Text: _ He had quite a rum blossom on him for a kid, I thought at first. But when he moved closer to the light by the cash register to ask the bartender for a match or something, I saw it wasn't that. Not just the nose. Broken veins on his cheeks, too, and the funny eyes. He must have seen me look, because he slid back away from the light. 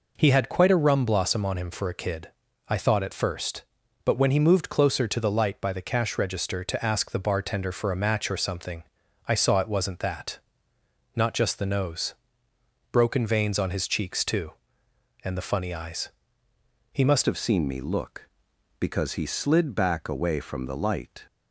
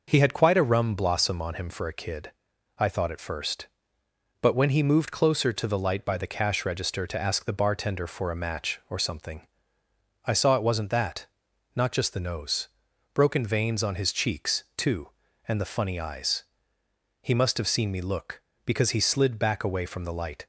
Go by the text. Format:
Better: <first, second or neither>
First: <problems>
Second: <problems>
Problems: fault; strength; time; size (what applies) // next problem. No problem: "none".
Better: second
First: changes voice at "have"; from 17.2 s on; 4.0 s long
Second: none